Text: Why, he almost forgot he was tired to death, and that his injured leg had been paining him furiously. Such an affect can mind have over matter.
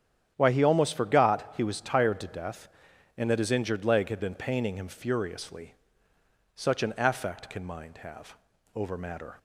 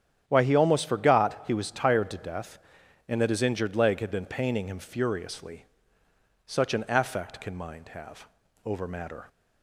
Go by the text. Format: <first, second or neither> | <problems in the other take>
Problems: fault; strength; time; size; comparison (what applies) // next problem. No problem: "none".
neither | starts louder than the rest; strong; the same in both // pauses between "have" and "over"; the same in both